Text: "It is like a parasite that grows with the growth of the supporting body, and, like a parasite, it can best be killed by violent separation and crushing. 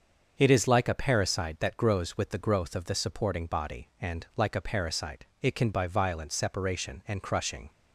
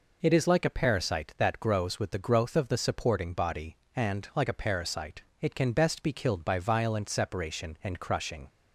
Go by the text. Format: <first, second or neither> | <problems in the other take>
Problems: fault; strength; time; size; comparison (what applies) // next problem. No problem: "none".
second | starts louder than the rest; until 1.3 s; 6.5 dB // skips "best be killed"; at 5.7 s